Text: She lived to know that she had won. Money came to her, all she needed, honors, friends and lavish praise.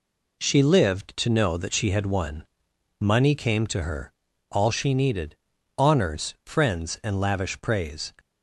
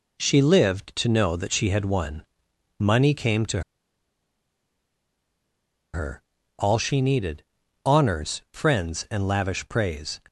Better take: first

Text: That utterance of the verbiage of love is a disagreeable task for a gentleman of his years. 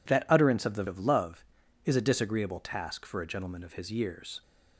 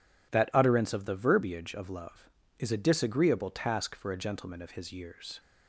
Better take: second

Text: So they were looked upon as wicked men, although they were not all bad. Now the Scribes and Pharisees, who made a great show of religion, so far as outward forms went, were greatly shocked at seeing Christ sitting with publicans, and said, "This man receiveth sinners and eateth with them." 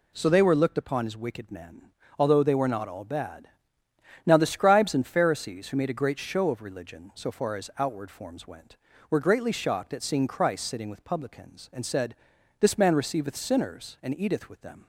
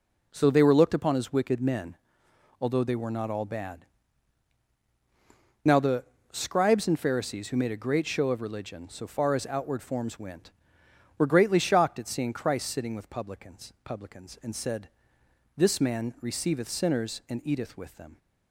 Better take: first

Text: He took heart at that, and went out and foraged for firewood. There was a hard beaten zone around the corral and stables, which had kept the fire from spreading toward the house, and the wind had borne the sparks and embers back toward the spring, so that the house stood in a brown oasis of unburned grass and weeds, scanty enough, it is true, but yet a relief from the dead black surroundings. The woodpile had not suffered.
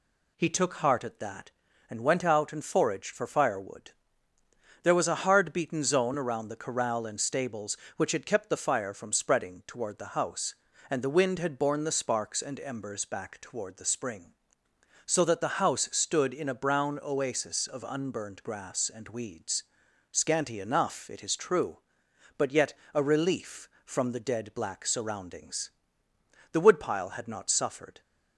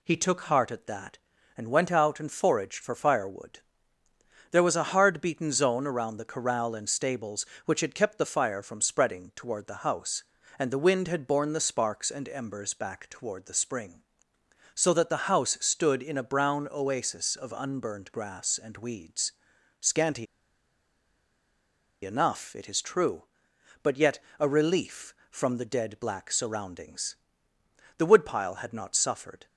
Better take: first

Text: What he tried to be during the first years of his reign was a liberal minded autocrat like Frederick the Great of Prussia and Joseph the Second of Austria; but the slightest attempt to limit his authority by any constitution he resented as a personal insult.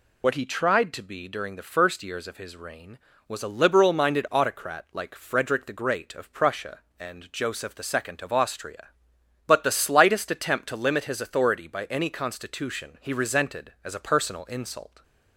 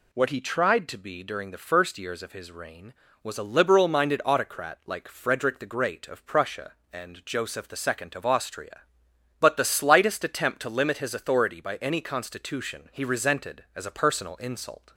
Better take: second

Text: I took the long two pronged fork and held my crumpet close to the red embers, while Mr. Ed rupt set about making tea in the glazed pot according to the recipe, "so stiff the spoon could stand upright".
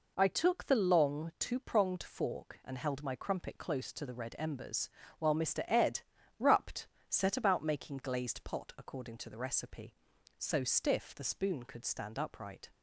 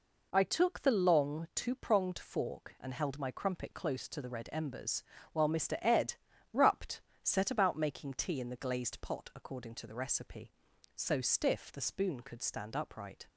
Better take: second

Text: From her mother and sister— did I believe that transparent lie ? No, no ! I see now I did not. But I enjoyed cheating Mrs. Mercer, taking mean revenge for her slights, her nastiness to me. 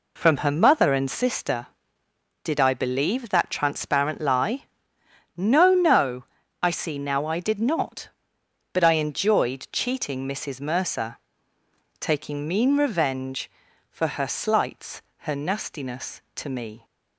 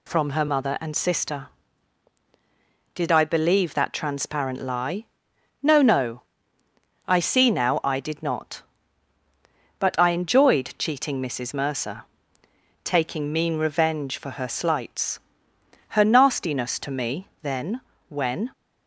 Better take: first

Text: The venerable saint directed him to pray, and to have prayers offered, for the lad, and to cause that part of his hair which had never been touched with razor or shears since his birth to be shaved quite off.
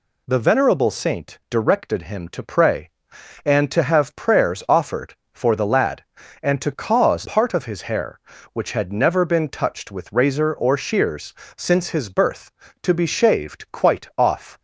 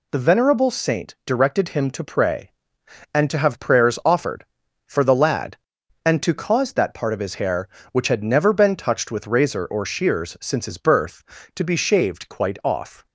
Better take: second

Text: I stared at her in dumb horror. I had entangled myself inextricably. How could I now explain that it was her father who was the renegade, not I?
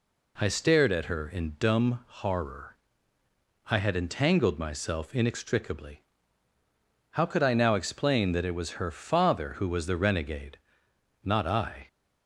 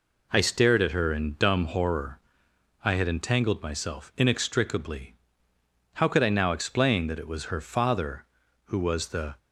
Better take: first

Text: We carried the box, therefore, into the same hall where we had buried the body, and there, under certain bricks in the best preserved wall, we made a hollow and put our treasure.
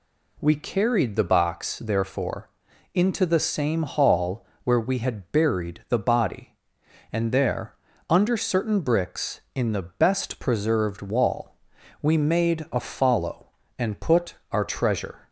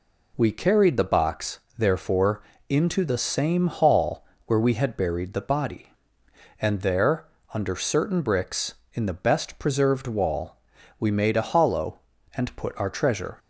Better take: second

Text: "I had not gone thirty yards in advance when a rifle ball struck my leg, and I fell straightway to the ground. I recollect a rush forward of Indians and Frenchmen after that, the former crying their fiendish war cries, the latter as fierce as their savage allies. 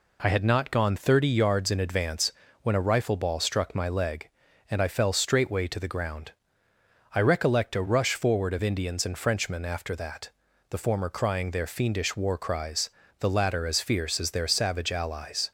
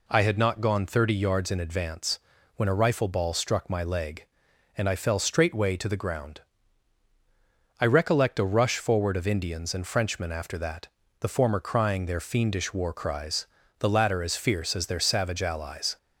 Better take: neither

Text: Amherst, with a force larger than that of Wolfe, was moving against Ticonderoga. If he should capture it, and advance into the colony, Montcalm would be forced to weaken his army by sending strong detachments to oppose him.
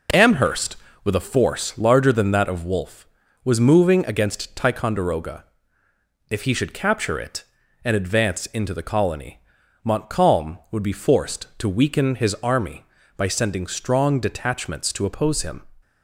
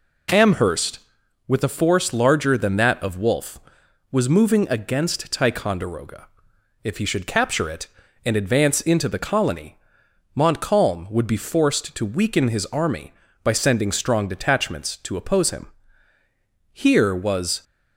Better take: first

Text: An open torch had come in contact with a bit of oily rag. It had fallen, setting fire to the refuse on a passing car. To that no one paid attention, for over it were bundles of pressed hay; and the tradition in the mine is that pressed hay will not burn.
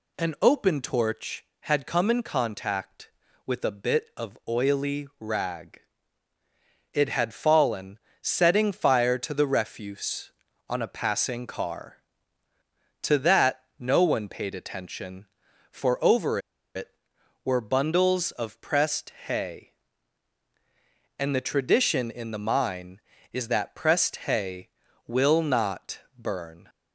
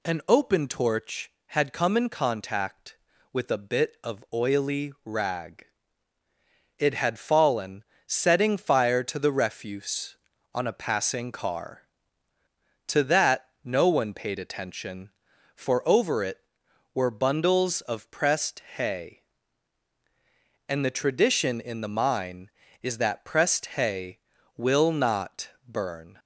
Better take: second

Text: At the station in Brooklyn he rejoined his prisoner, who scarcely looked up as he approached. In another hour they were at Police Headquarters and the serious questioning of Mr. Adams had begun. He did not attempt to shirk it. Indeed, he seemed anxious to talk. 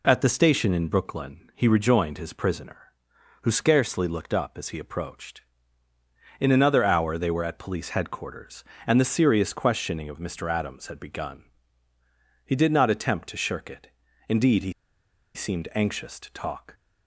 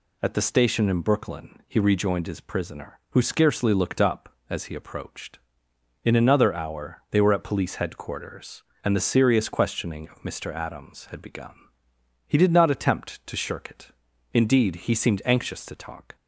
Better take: second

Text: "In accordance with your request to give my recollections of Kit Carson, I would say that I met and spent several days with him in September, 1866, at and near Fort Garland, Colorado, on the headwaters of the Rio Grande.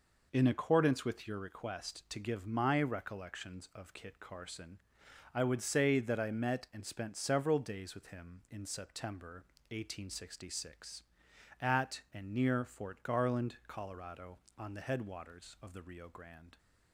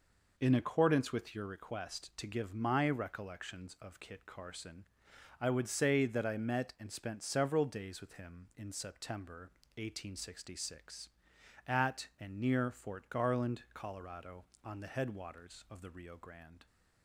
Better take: neither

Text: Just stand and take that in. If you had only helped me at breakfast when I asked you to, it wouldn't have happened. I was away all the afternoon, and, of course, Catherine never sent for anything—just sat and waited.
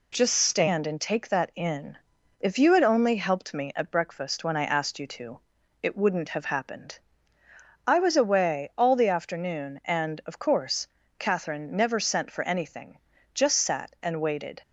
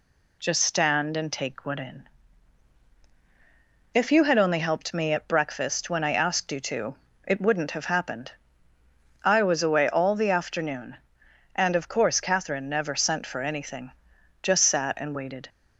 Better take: first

